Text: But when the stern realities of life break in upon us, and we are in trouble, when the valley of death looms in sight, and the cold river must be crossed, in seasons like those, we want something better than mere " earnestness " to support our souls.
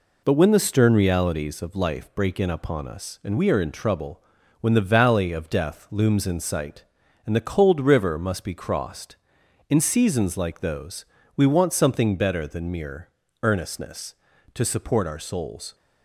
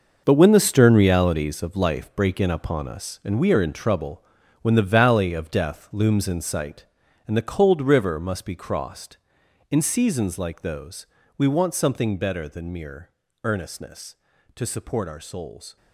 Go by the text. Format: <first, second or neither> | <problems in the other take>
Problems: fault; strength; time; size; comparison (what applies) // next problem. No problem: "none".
first | gets quieter; strong; throughout; 15 dB